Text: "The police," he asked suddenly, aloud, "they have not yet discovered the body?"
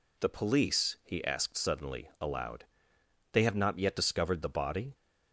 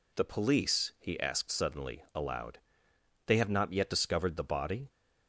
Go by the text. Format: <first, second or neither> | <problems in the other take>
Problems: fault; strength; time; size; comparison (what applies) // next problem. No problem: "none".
neither | none